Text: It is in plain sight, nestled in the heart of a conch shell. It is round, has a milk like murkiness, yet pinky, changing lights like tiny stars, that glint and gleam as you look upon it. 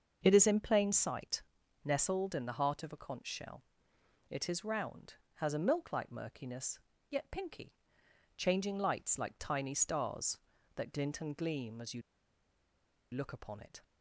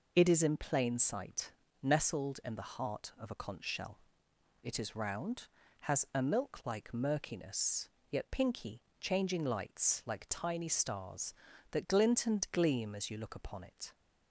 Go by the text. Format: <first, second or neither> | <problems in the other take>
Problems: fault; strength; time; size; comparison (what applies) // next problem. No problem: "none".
second | starts louder than the rest; until 1.2 s; 6.5 dB // pauses between "you" and "look"; at 12.0 s; 1.1 s long